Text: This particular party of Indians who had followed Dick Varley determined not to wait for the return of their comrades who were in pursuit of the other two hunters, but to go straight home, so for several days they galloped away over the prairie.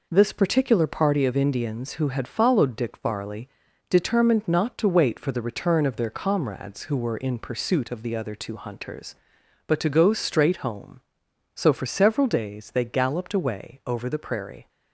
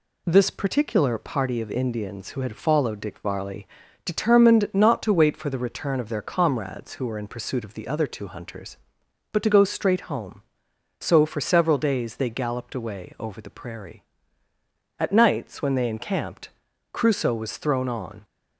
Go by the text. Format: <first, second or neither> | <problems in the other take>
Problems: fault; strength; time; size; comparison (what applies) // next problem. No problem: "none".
first | pauses between "Varley" and "determined"; at 3.6 s; 0.38 s long; also in the first // goes on to say "At nights when they encamped Crusoe was thrown on"; strong; from 14.9 s on; 3.2 s long